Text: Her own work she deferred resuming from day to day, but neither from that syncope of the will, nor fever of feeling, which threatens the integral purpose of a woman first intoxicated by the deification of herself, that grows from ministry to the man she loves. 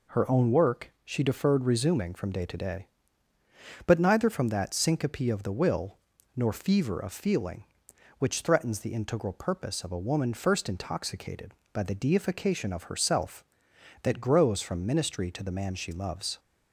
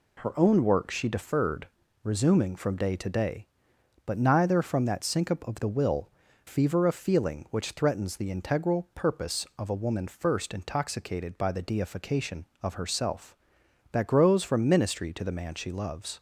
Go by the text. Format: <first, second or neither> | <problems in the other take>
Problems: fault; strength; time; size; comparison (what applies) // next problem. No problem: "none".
first | pauses between "deferred" and "resuming"; slight; at 1.6 s; 0.36 s long // skips "nor"; at 6.2 s